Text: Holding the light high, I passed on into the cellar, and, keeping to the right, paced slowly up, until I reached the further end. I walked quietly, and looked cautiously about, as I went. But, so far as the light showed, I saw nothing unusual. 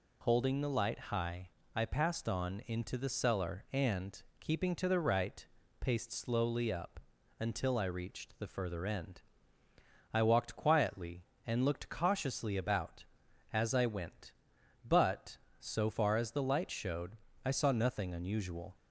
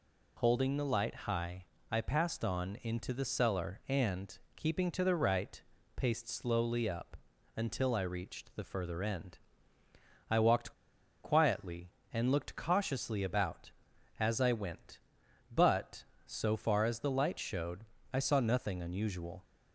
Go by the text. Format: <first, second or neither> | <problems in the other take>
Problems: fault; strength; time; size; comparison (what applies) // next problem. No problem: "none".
first | pauses between "walked" and "quietly"; noticeable; at 10.7 s; 0.52 s long